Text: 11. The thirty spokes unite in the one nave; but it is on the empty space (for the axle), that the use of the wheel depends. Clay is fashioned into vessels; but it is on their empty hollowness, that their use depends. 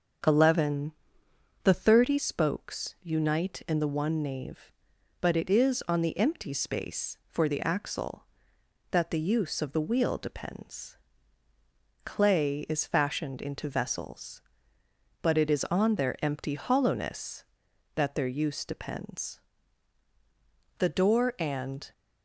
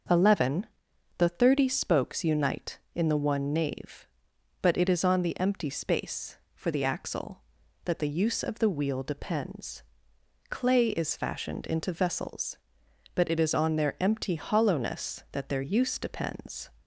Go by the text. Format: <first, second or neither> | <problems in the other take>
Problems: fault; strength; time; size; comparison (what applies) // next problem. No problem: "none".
second | starts louder than the rest; until 2.0 s; 7 dB; also in the second // goes on to say "The door and"; noticeable; from 20.7 s on; 1.1 s long